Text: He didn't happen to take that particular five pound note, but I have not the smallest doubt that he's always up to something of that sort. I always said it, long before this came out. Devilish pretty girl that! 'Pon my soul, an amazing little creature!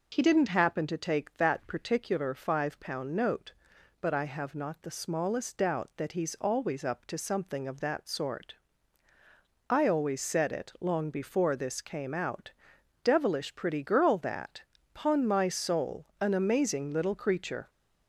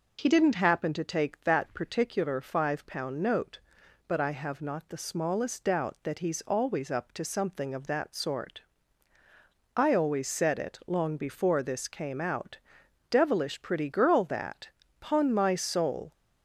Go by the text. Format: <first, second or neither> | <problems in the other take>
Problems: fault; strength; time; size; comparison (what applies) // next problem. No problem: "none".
first | stops before "an amazing little creature"; at 16.1 s